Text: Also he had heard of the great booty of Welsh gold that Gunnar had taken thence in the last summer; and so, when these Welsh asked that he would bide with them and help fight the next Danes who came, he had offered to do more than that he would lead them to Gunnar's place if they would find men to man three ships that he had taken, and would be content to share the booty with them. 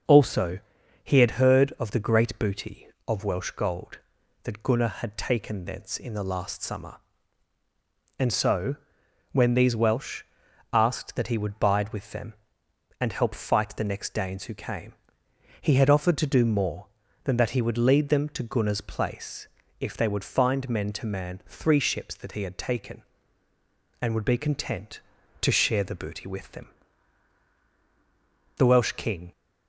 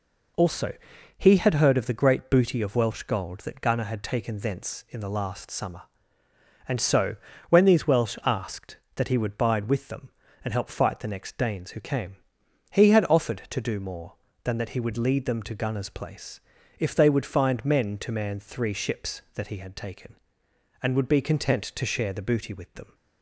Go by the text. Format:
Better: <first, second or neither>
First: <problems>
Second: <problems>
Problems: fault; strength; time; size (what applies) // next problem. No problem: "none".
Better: second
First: starts louder than the rest; until 1.5 s; 6.5 dB // pauses between "Also" and "he"; at 0.5 s; 0.44 s long // pauses between "Welsh" and "asked"; noticeable; at 10.2 s; 0.50 s long // pauses between "place" and "if"; slight; at 19.4 s; 0.32 s long // goes on to say "The Welsh king"; noticeable; from 28.5 s on; 0.74 s long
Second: pauses between "Also" and "he"; at 0.7 s; 0.42 s long // pauses between "place" and "if"; at 16.4 s; 0.40 s long